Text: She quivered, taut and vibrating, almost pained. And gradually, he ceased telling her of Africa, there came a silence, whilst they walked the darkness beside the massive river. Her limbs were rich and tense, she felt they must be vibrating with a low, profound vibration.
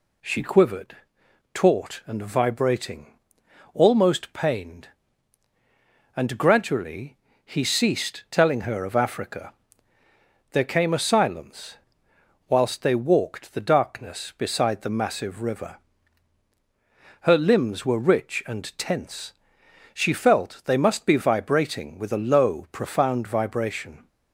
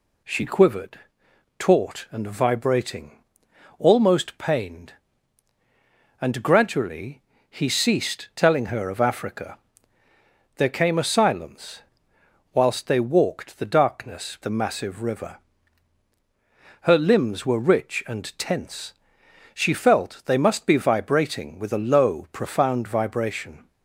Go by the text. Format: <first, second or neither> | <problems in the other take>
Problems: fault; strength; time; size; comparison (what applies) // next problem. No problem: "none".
first | skips "beside"; at 14.3 s